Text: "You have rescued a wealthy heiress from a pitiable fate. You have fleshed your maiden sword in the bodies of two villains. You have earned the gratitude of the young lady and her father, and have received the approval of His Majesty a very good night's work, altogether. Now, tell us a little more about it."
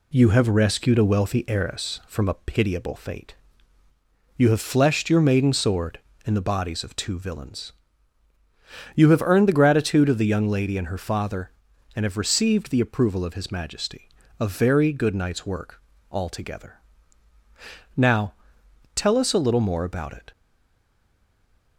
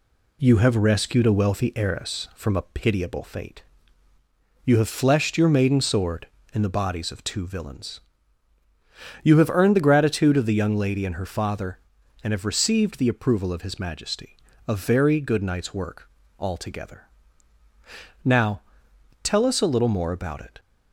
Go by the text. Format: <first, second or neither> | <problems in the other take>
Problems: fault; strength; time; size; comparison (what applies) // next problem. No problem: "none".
second | pauses between "Majesty" and "a"; slight; at 14.1 s; 0.28 s long; slight in the second // stays silent after the last word; noticeable; from 20.3 s on; 1.4 s long